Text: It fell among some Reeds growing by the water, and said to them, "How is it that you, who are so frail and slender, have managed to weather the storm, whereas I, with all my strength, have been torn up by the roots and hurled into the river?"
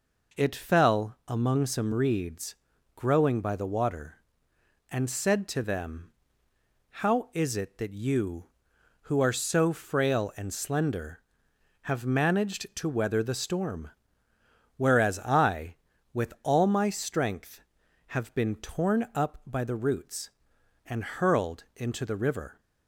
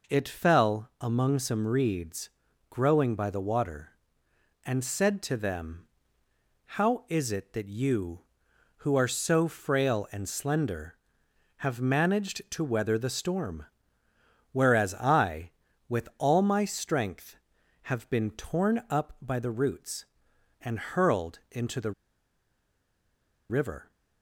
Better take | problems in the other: first | pauses between "Reeds" and "growing"; at 2.2 s; 0.40 s long; also in the first // pauses between "the" and "river"; strong; at 21.9 s; 1.5 s long

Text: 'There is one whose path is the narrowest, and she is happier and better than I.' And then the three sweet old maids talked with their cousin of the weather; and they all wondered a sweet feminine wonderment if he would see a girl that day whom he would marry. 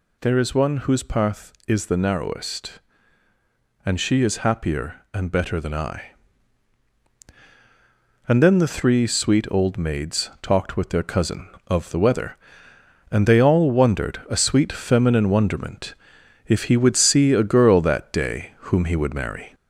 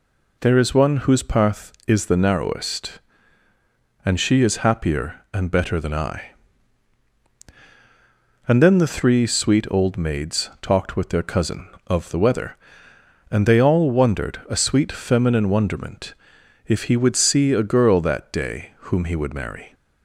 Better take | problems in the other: second | gets louder; slight; throughout; 2.5 dB // pauses between "wonderment" and "if"; noticeable; at 15.9 s; 0.54 s long; noticeable in the second

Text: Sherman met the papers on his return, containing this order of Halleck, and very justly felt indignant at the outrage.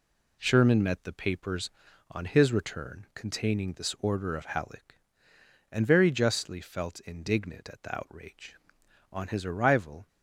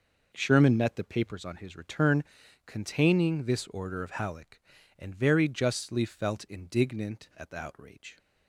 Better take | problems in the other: second | goes on to say "On his arrival"; noticeable; from 9.1 s on; 0.94 s long

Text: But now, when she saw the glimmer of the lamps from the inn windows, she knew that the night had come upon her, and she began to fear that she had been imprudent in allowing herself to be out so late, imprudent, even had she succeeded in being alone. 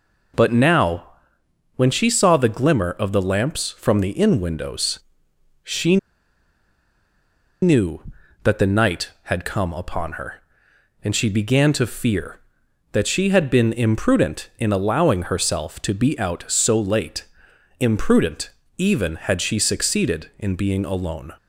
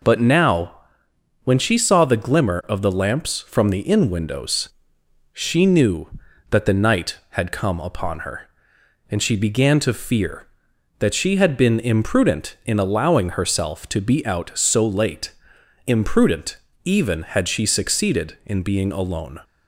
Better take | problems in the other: second | pauses between "she" and "knew"; strong; at 5.9 s; 1.6 s long

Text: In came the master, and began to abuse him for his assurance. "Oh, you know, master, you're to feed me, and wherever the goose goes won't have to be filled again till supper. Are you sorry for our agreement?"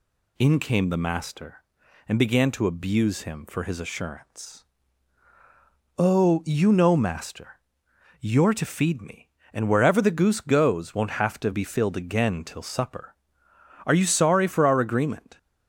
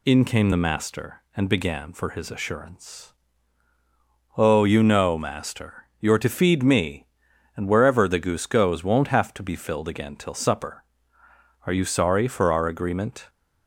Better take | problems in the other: first | skips "to abuse him"; at 1.9 s

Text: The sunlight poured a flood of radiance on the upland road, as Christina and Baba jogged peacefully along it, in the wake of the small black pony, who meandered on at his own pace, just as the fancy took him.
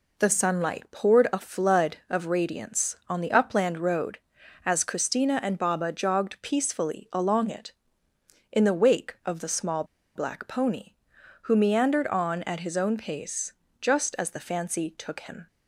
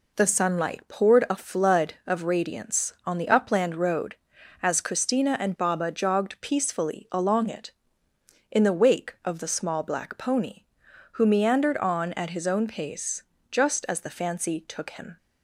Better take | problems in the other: second | pauses between "small" and "black"; slight; at 9.8 s; 0.32 s long

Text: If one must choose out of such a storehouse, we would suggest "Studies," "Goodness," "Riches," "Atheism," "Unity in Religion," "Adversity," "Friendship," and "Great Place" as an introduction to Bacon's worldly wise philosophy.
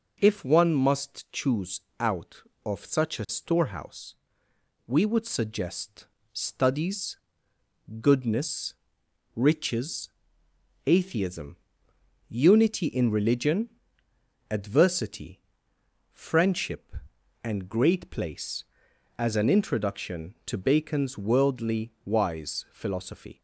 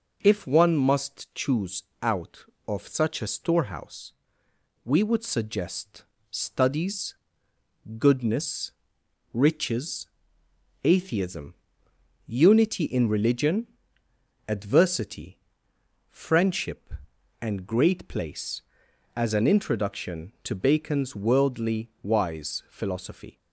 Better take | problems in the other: neither | pauses between "choose" and "out"; slight; the same in both // pauses between "suggest" and "Studies"; slight; the same in both

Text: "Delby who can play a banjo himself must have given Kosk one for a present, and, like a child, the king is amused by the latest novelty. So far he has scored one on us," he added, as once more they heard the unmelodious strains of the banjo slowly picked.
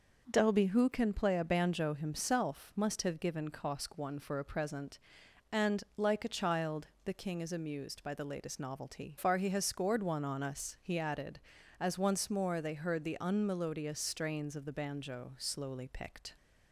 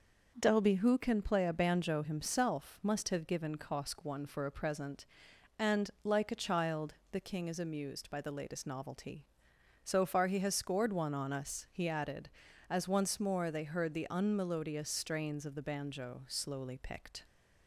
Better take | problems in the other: second | skips "So"; at 9.1 s

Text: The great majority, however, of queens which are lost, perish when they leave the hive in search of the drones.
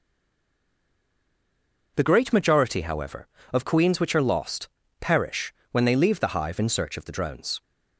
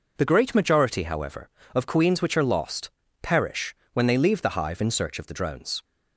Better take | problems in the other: second | stays silent before the first word; noticeable; until 1.9 s; 1.9 s long // pauses between "perish" and "when"; slight; at 5.5 s; 0.16 s long; slight in the second

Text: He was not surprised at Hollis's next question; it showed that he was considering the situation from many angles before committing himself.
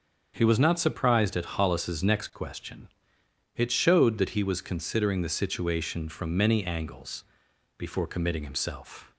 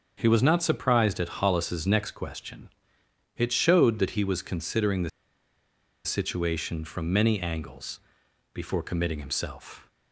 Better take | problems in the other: first | starts louder than the rest; until 1.1 s; 7 dB; also in the first // pauses between "the" and "situation"; noticeable; at 5.0 s; 0.95 s long // pauses between "angles" and "before"; noticeable; at 7.9 s; 0.52 s long; noticeable in the first

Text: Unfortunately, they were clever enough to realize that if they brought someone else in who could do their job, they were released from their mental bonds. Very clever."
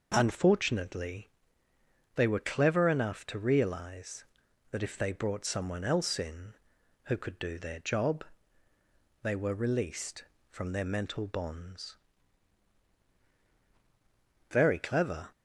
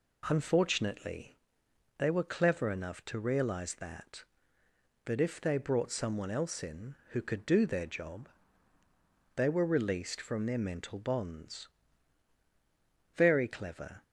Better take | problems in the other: first | says "that" twice; at 5.0 s

